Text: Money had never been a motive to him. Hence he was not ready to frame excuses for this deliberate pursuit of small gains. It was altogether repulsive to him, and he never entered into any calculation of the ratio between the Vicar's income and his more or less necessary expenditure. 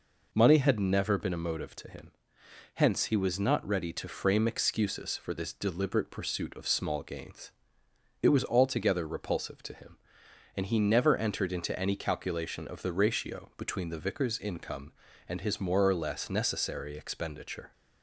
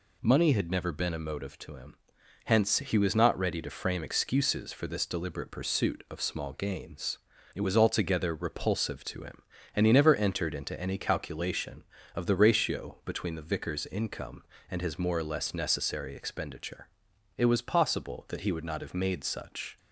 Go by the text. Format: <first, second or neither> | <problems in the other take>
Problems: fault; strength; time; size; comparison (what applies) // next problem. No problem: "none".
first | goes on to say "It was possible that he would not have made such"; strong; from 17.3 s on; 2.4 s long